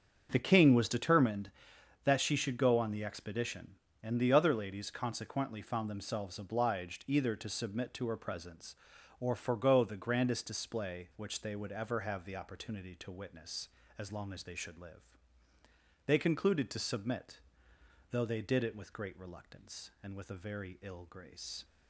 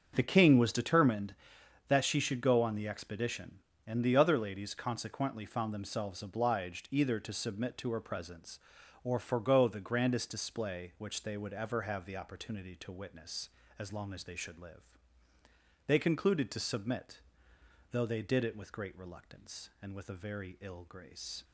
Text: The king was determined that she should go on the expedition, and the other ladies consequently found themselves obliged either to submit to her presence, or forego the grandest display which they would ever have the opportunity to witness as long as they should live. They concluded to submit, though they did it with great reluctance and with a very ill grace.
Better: neither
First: starts louder than the rest; strong; until 1.3 s; 7 dB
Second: starts louder than the rest; strong; until 1.1 s; 7 dB

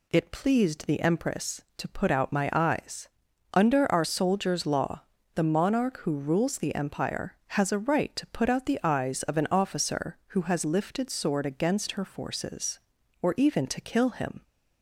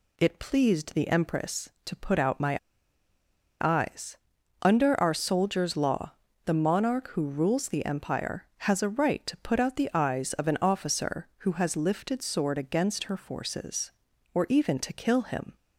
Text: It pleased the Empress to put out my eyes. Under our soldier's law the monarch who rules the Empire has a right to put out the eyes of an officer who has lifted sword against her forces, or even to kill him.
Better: first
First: pauses between "law" and "the"; slight; at 5.0 s; 0.32 s long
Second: pauses between "my" and "eyes"; at 2.5 s; 1.0 s long // pauses between "law" and "the"; slight; at 6.1 s; 0.32 s long

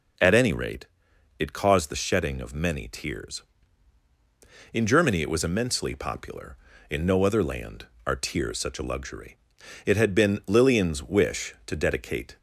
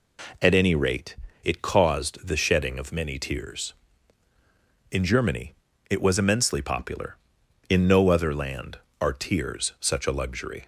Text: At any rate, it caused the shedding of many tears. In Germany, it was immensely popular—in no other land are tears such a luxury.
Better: second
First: goes on to say "It had been Lillian's wish to dedicate"; strong; from 9.8 s on; 2.5 s long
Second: none

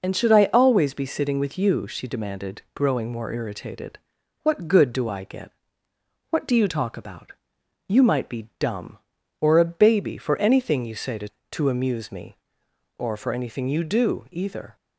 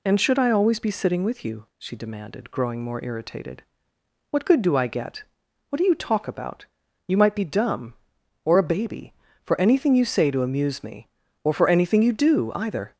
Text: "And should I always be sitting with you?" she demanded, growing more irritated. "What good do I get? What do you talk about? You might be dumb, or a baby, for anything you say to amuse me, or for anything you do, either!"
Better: second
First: says "to" twice; at 11.5 s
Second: none

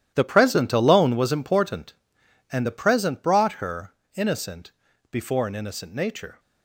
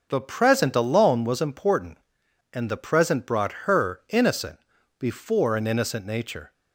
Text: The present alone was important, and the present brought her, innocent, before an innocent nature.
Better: second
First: gets quieter; strong; throughout; 13 dB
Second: none

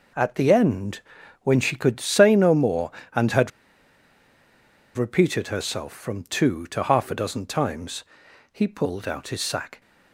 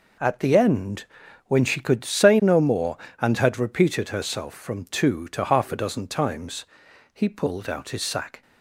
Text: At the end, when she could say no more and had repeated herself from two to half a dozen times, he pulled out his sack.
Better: second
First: pauses between "had" and "repeated"; strong; at 3.5 s; 1.4 s long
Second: none

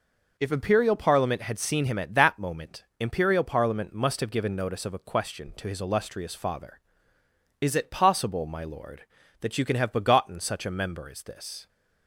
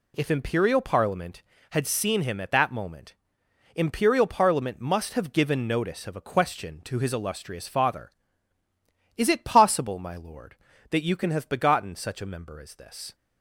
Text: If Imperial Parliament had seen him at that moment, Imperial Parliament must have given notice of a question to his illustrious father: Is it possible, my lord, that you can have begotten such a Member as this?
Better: neither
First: none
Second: none

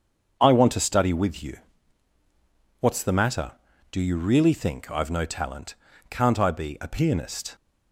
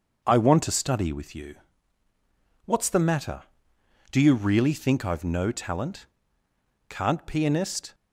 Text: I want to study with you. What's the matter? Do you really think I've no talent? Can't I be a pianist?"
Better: first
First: starts louder than the rest; until 1.4 s; 7 dB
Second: starts louder than the rest; until 1.2 s; 6.5 dB // skips "I be a"; at 7.2 s

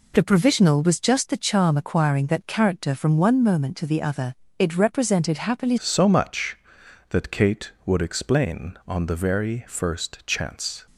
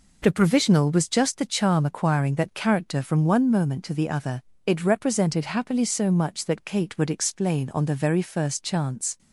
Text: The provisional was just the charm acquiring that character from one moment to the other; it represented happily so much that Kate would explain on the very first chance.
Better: second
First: changes voice at "so"; from 5.7 s on; 5.1 s long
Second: none

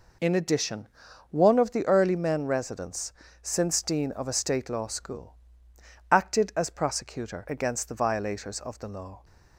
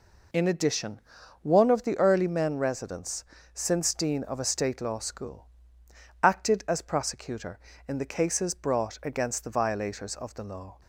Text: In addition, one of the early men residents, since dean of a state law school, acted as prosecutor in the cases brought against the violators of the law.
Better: second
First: skips "in the cases brought"; at 7.4 s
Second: none

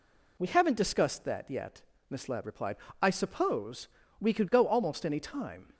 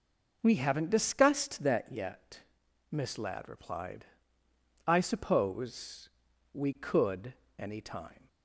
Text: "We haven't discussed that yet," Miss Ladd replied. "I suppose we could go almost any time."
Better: first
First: pauses between "suppose" and "we"; slight; at 3.8 s; 0.32 s long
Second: pauses between "suppose" and "we"; noticeable; at 6.0 s; 0.46 s long // skips "go almost"; at 7.4 s

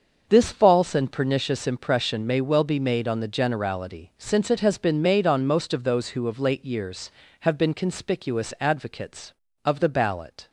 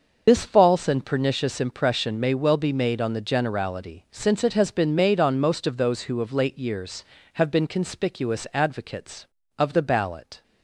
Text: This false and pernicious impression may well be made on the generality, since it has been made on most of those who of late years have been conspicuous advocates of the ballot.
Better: first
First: starts louder than the rest; until 1.3 s; 6.5 dB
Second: loses the start of "This"; at 0.2 s; 50 ms // starts louder than the rest; noticeable; until 1.2 s; 6 dB

